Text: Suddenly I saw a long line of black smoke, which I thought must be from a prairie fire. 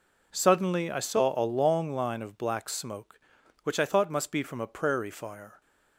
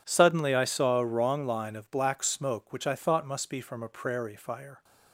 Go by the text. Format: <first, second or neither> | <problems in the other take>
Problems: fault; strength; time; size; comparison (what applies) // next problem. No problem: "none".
first | says "wrong" for "long"; at 1.0 s